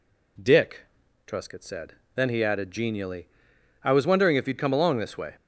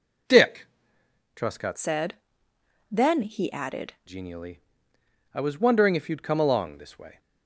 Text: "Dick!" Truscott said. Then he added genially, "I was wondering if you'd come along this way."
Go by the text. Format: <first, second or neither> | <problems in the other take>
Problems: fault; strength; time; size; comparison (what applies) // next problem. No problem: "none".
first | changes voice from "said" to "added"; from 1.7 to 3.9 s; 2.2 s long